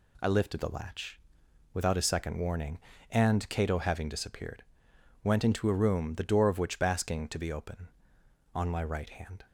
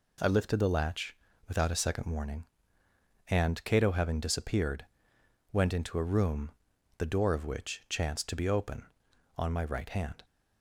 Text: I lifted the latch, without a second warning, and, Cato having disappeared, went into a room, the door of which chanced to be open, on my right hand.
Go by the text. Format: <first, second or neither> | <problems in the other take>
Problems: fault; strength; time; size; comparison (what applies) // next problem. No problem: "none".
second | says "basking" for "chanced"; at 6.7 s